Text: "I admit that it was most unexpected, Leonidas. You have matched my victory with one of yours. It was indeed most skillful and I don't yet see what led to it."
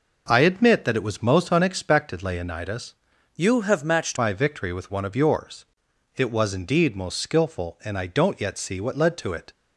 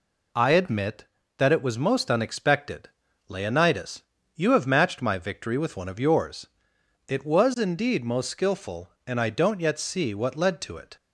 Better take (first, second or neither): second